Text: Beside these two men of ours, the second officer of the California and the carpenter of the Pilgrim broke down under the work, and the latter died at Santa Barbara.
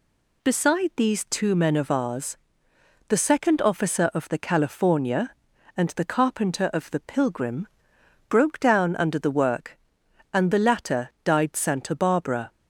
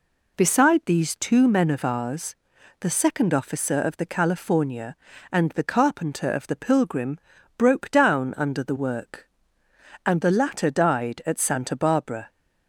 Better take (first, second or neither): second